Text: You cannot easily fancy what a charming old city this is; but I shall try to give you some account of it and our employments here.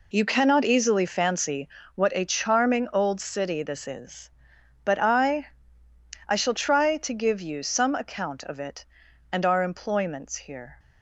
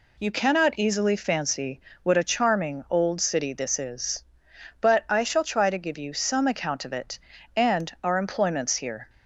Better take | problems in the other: second | pauses between "fancy" and "what"; slight; at 1.6 s; 0.26 s long; slight in the second // says "I" twice; at 6.2 s

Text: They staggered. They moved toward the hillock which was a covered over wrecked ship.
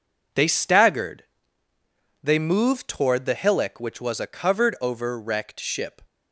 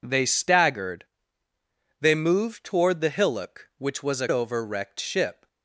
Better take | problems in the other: first | skips "covered"; at 4.2 s

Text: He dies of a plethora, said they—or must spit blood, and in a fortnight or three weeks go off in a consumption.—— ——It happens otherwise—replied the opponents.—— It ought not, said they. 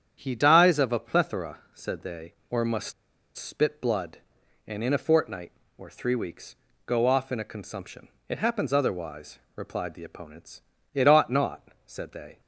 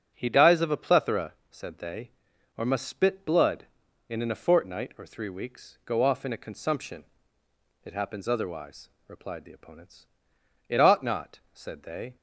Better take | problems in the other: second | starts louder than the rest; strong; until 1.2 s; 9 dB; also in the second // pauses between "must" and "spit"; at 2.9 s; 0.45 s long // pauses between "weeks" and "go"; slight; at 6.5 s; 0.32 s long

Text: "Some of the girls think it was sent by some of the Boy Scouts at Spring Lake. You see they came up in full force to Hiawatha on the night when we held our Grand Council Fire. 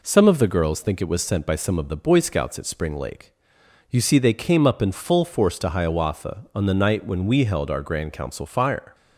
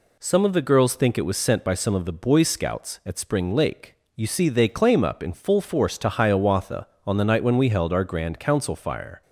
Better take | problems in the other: first | says "claim" for "came"; at 4.6 s

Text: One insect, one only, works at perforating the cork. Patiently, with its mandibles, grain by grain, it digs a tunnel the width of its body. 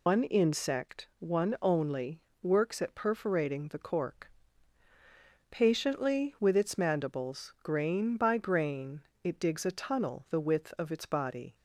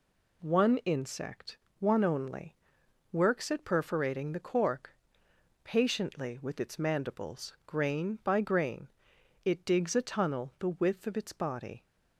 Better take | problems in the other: second | loses the start of "One"; at 0.0 s; 125 ms

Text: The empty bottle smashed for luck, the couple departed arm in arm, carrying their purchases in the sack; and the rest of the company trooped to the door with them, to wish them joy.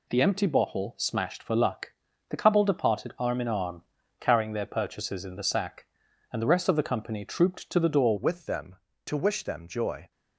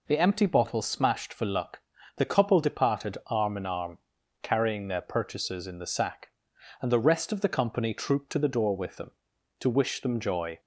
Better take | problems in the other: second | changes voice at "with"; from 8.1 s on; 2.0 s long

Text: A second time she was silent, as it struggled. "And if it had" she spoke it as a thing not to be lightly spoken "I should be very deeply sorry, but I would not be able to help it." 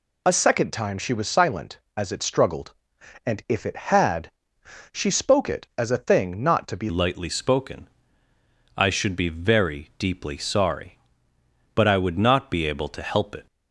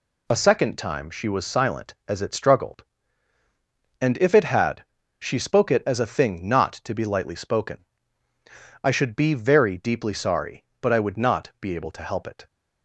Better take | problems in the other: second | pauses between "had" and "she"; noticeable; at 4.2 s; 0.62 s long; slight in the second // changes voice at "lightly"; from 6.9 s on; 6.5 s long // pauses between "spoken" and "I"; noticeable; at 7.8 s; 0.88 s long; noticeable in the second

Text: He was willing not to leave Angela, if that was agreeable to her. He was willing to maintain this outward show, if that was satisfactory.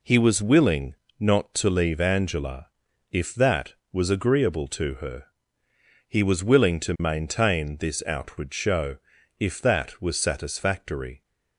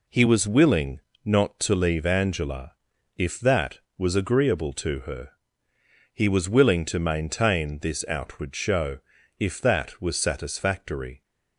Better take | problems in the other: neither | pauses between "willing" and "not"; slight; the same in both

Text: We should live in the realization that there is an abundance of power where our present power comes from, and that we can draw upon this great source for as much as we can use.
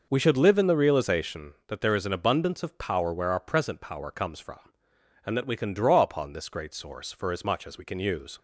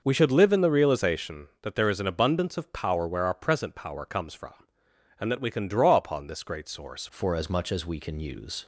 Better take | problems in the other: first | changes voice at "for"; from 7.0 s on; 1.6 s long

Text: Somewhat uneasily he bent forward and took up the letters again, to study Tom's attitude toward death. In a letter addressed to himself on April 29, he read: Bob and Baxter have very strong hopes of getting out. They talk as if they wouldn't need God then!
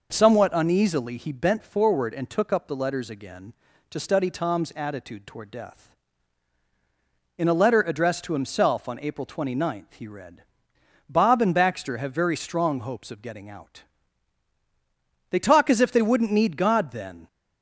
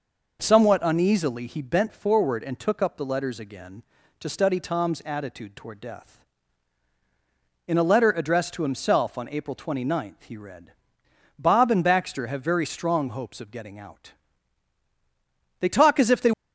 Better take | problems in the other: first | stops before "wouldn't need God then"; at 16.3 s

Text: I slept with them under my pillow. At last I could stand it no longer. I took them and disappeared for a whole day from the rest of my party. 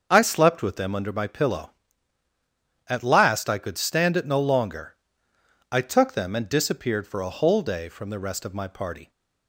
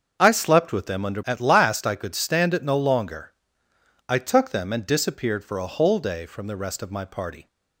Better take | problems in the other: first | starts louder than the rest; until 1.2 s; 6.5 dB; also in the first // skips "my pillow"; at 1.2 s

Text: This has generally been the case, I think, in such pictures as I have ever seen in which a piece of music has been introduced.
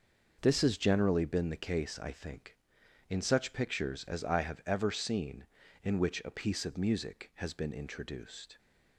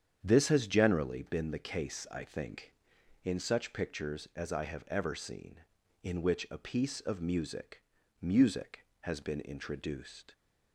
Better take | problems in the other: first | starts louder than the rest; strong; until 1.2 s; 8.5 dB // says "music" twice; at 8.2 s

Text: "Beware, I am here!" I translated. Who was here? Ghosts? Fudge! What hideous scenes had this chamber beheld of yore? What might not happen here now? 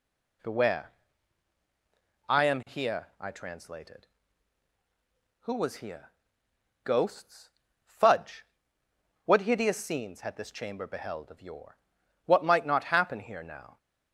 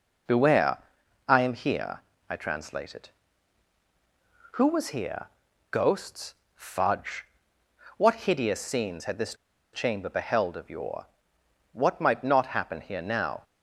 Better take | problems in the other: first | pauses between "this" and "chamber"; at 9.3 s; 0.38 s long

